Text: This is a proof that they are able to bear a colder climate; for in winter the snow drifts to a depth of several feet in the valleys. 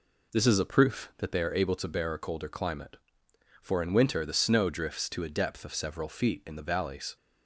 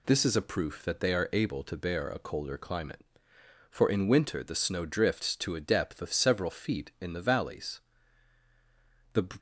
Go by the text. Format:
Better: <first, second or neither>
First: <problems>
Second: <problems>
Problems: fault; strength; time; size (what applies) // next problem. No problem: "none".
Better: first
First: none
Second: goes on to say "The"; slight; from 9.1 s on; 0.12 s long